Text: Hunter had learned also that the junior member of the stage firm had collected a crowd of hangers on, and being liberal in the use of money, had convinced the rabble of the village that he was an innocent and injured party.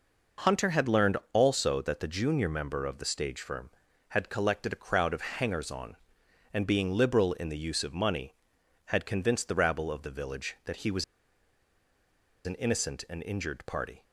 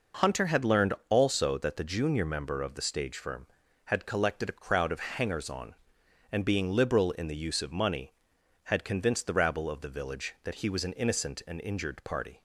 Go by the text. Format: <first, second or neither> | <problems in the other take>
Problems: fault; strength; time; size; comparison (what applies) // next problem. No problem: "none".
second | pauses between "learned" and "also"; slight; at 1.1 s; 0.16 s long; slight in the second // pauses between "was" and "an"; strong; at 11.0 s; 1.4 s long